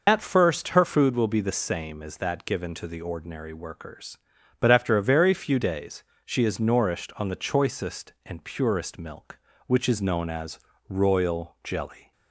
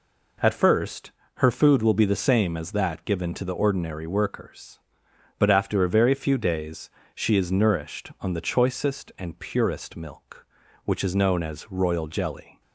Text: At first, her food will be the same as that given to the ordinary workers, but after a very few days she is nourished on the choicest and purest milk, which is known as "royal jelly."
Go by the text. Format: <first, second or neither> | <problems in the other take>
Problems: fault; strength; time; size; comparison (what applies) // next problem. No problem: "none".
second | loses the start of "At"; at 0.0 s; 70 ms // pauses between "days" and "she"; slight; at 6.0 s; 0.20 s long; slight in the second // pauses between "as" and "royal"; slight; at 10.5 s; 0.28 s long